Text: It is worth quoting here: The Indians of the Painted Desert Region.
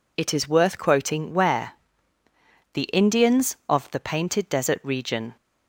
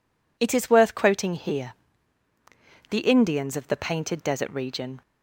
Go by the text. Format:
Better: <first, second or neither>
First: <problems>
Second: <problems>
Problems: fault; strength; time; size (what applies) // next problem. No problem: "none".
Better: second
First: says "where" for "here"; at 1.3 s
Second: none